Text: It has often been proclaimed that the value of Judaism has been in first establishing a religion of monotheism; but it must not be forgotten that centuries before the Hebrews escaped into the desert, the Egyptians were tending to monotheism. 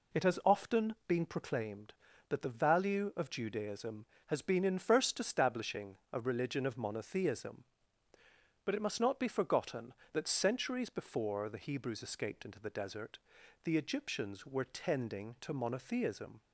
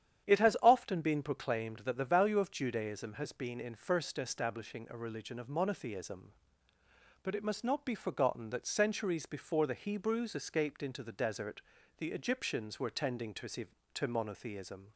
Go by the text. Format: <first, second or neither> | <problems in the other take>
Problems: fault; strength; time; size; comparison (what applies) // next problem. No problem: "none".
first | starts louder than the rest; strong; until 1.3 s; 9.5 dB // says "to" twice; at 13.9 s